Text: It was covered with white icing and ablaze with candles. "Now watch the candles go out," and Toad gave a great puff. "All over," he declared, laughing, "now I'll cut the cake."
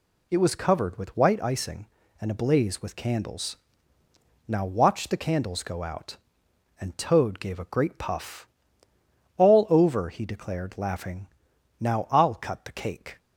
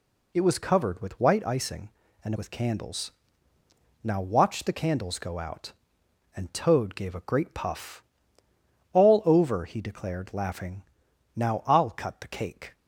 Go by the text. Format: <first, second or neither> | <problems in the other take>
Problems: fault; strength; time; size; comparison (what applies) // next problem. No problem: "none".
first | skips "ablaze"; at 2.3 s